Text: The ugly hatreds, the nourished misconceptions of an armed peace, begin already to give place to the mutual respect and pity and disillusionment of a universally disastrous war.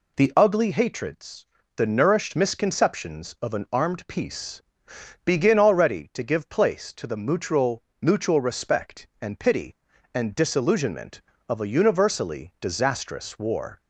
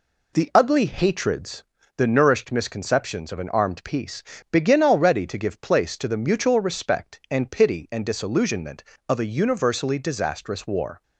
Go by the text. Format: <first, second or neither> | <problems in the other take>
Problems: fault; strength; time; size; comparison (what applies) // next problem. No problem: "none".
second | says "mutual" twice; at 8.0 s